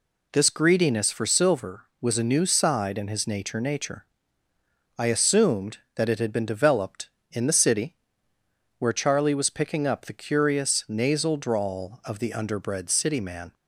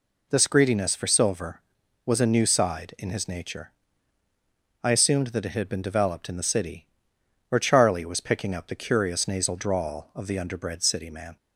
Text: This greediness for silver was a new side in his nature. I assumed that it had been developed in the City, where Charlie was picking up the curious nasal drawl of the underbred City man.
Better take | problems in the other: second | says "nature" twice; at 3.5 s

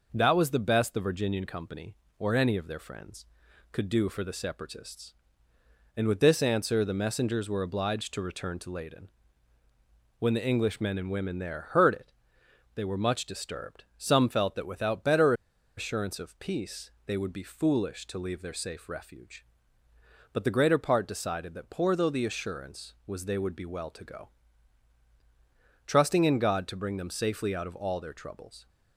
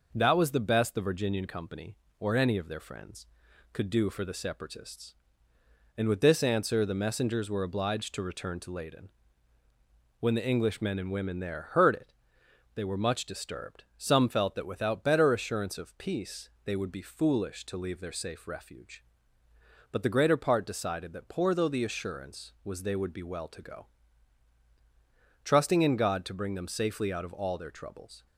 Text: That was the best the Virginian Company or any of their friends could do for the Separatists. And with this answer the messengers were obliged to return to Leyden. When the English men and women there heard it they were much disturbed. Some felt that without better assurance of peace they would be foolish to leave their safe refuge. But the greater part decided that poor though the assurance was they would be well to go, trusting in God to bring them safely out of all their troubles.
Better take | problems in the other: second | pauses between "it" and "they"; noticeable; at 12.1 s; 0.62 s long; noticeable in the second // pauses between "better" and "assurance"; at 15.3 s; 0.44 s long // pauses between "peace" and "they"; slight; at 16.9 s; 0.16 s long; slight in the second

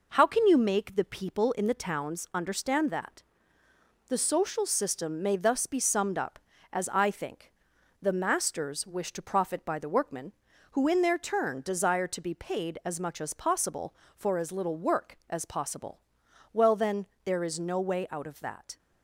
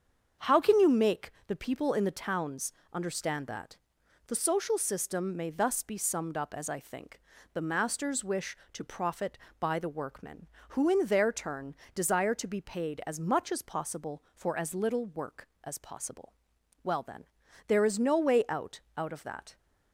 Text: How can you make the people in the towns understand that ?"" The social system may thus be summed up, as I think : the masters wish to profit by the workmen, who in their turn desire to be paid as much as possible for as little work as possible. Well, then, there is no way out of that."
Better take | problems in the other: first | starts louder than the rest; strong; until 1.6 s; 7 dB // pauses between "make" and "the"; slight; at 1.3 s; 0.16 s long // pauses between "towns" and "understand"; slight; at 2.7 s; 0.22 s long // pauses between "turn" and "desire"; slight; at 11.7 s; 0.18 s long // says "out" twice; at 18.9 s

